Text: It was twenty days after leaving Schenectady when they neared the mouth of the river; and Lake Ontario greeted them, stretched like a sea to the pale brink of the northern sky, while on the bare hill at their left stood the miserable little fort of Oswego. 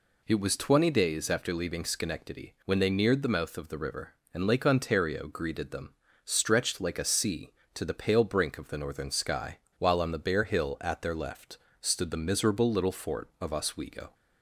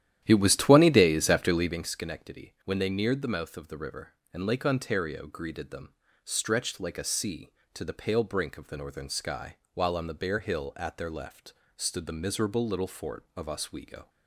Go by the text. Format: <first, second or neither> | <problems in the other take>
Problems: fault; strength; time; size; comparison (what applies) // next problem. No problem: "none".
first | starts louder than the rest; strong; until 1.9 s; 11.5 dB // pauses between "left" and "stood"; slight; at 11.5 s; 0.22 s long; slight in the first